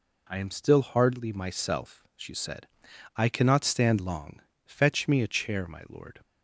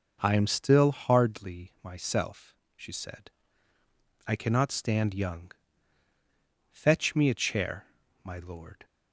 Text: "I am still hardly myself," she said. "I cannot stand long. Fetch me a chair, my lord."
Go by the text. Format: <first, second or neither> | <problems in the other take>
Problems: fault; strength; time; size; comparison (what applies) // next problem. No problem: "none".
first | says "young" for "long"; at 5.1 s